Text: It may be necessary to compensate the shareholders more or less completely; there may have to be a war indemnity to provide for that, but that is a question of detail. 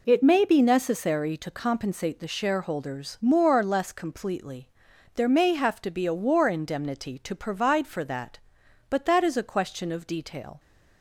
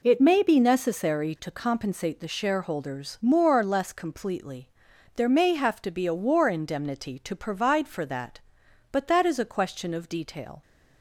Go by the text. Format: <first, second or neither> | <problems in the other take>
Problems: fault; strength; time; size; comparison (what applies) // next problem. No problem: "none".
neither | none